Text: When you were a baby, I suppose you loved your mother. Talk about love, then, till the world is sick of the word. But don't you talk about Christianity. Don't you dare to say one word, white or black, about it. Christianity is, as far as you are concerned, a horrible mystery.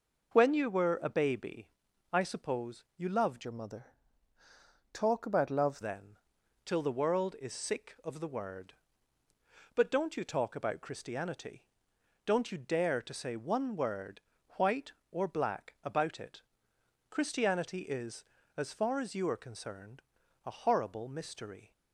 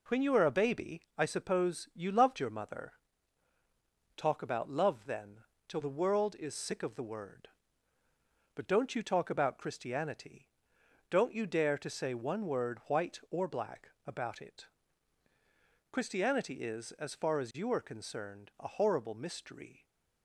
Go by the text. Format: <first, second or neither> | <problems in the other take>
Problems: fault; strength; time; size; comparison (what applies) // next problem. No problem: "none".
second | changes voice from "your" to "love"; from 3.4 to 5.8 s; 2.4 s long